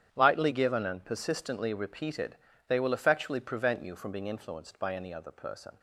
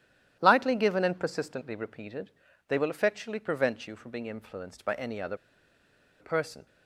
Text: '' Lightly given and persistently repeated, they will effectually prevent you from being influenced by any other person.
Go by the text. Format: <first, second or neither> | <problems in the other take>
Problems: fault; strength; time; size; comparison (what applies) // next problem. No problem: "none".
first | starts louder than the rest; strong; until 1.4 s; 11.5 dB; strong in the first // pauses between "other" and "person"; noticeable; at 5.3 s; 0.84 s long